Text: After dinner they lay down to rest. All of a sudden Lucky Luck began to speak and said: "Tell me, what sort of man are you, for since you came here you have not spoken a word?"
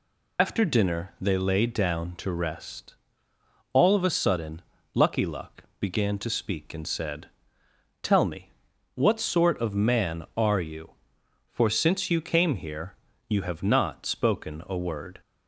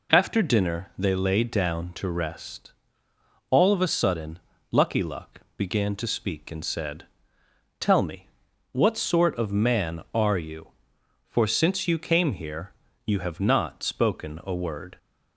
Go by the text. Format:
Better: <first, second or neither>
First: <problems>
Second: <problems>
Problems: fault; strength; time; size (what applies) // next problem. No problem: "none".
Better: second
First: loses the start of "After"; at 0.3 s; 75 ms // pauses between "sudden" and "Lucky"; slight; at 4.6 s; 0.32 s long // pauses between "here" and "you"; slight; at 12.9 s; 0.34 s long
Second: pauses between "sudden" and "Lucky"; slight; at 4.4 s; 0.32 s long // pauses between "here" and "you"; slight; at 12.7 s; 0.34 s long